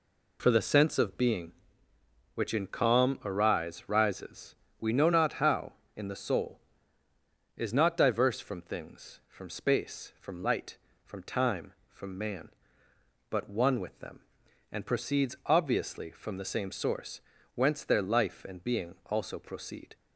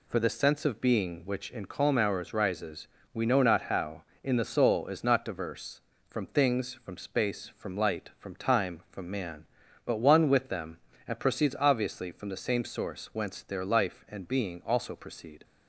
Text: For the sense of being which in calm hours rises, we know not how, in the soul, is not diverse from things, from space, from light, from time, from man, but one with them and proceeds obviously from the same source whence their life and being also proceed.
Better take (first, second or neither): second